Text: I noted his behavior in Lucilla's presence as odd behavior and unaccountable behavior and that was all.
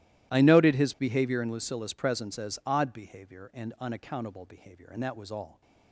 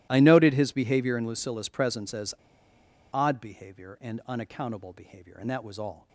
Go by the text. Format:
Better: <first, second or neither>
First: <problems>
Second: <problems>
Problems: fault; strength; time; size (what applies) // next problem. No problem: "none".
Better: first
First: none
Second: starts louder than the rest; strong; until 1.1 s; 15 dB // pauses between "as" and "odd"; noticeable; at 2.3 s; 0.80 s long